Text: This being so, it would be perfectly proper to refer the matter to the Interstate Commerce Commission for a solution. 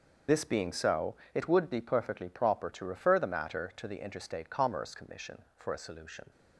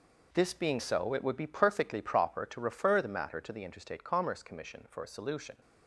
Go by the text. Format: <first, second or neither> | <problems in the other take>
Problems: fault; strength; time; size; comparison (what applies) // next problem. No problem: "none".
second | loses the start of "This"; at 0.2 s; 40 ms